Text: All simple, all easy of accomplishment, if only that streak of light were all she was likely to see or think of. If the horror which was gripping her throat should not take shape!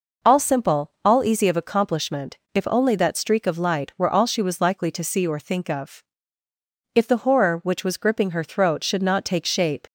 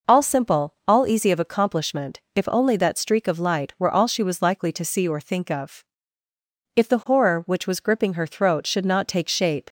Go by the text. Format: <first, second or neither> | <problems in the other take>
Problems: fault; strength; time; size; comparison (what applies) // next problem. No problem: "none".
neither | none